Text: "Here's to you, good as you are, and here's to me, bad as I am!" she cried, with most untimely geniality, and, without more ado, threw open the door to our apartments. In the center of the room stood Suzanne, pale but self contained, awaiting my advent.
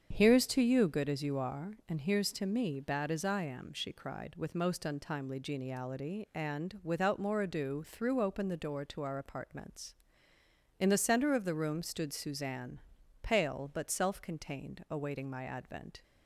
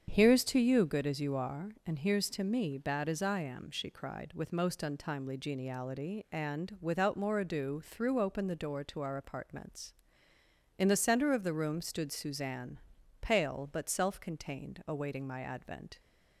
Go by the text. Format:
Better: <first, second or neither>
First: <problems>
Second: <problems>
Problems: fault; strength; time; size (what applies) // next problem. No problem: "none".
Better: neither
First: starts louder than the rest; strong; until 1.1 s; 7.5 dB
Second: starts louder than the rest; strong; until 1.1 s; 7.5 dB